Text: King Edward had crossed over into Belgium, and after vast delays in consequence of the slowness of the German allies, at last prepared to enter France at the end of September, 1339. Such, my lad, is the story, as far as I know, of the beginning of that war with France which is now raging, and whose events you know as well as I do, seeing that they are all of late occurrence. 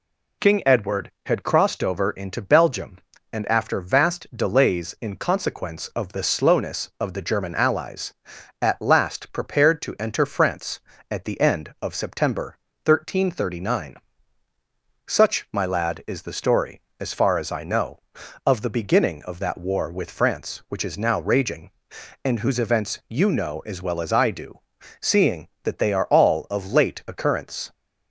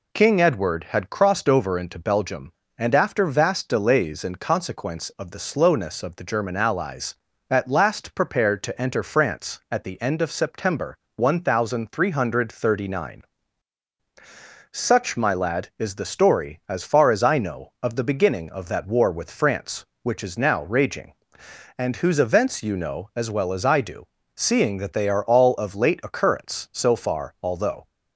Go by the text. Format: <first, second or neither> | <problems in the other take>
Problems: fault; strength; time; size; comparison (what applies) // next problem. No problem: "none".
first | goes on to say "So far although"; noticeable; from 26.7 s on; 1.1 s long